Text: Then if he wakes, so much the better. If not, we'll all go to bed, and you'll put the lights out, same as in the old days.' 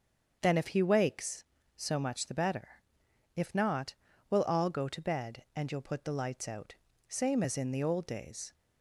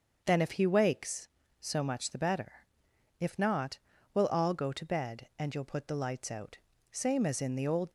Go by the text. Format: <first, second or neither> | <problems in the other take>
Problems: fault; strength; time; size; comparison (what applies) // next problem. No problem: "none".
first | starts louder than the rest; until 1.2 s; 6.5 dB; also in the first // stops before "days"; at 7.8 s